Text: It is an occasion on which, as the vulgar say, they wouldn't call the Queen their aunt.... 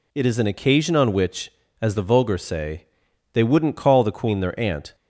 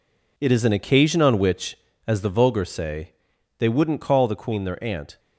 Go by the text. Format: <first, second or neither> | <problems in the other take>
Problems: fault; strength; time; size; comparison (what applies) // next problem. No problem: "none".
first | gets quieter; strong; throughout; 8 dB